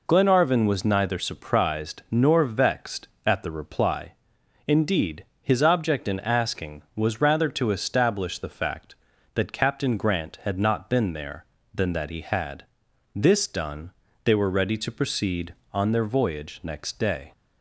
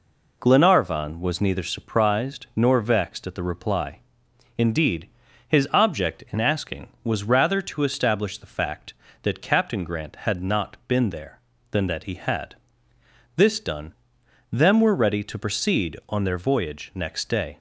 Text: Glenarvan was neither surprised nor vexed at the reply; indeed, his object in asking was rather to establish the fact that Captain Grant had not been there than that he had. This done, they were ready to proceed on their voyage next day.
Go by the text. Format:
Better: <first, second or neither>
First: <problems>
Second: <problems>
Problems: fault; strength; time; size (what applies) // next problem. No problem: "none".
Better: first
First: none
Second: says "them" for "they"; at 14.4 s